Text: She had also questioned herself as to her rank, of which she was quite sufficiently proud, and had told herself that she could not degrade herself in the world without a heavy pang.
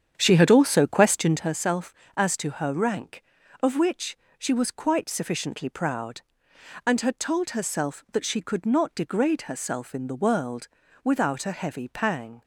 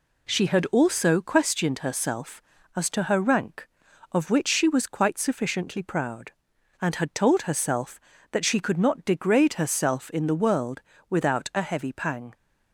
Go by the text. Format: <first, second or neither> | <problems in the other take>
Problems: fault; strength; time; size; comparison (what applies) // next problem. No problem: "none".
second | starts louder than the rest; strong; until 1.5 s; 8.5 dB // pauses between "which" and "she"; slight; at 4.1 s; 0.22 s long // pauses between "world" and "without"; slight; at 10.6 s; 0.34 s long; slight in the second